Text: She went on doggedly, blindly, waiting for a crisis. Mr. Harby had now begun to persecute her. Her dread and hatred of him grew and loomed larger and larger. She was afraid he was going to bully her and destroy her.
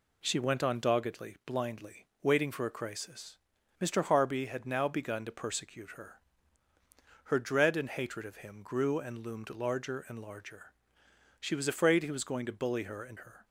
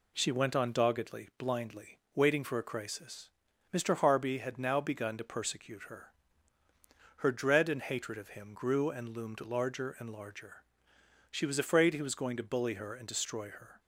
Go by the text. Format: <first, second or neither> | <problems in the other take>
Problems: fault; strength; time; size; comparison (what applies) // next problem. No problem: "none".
second | skips "destroy"; at 13.1 s